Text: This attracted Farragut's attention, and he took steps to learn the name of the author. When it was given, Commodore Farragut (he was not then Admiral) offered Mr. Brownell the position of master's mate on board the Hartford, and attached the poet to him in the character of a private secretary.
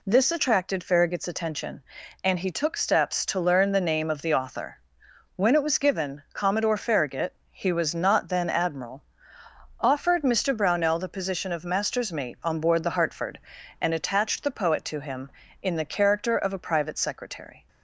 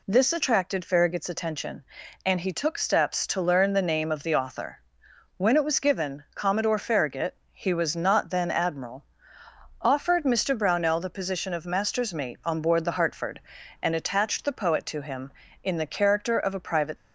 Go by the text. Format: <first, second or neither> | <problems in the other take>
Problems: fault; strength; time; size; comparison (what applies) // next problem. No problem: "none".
first | stops before "secretary"; at 16.9 s